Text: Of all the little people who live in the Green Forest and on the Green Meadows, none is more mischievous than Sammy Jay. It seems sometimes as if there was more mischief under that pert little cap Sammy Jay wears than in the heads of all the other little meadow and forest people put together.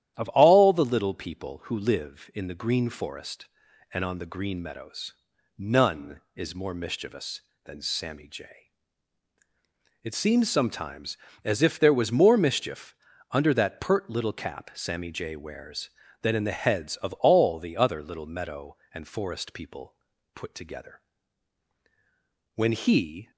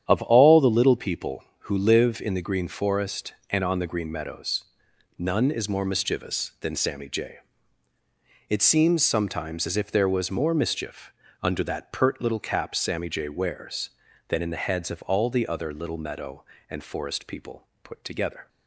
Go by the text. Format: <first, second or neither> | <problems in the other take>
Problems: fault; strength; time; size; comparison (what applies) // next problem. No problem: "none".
second | starts louder than the rest; strong; until 1.1 s; 11.5 dB; strong in the second // pauses between "mischief" and "under"; at 12.9 s; 0.38 s long; slight in the second // pauses between "people" and "put"; at 19.9 s; 0.42 s long; slight in the second // goes on to say "When he"; noticeable; from 22.5 s on; 0.76 s long